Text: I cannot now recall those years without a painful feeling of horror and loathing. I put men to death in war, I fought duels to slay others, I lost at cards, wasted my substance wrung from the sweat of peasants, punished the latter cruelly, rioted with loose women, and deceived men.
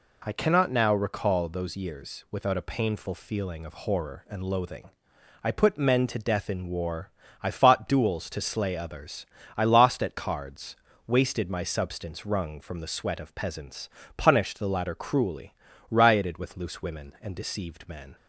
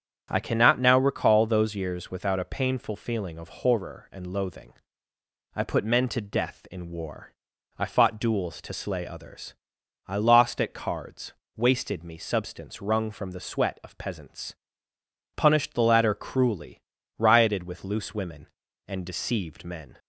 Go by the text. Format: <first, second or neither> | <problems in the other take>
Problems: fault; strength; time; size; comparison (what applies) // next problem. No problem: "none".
first | starts louder than the rest; strong; until 1.3 s; 8.5 dB // says "me" for "my"; at 12.0 s